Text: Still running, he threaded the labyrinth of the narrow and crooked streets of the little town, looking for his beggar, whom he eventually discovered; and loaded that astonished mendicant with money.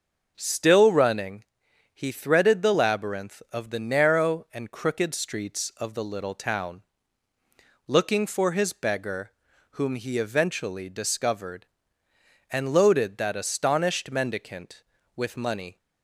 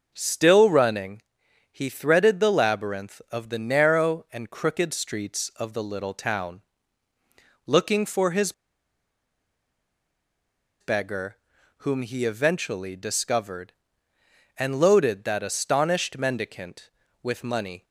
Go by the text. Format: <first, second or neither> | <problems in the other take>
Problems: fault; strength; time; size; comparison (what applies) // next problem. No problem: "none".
first | pauses between "his" and "beggar"; strong; at 8.5 s; 2.2 s long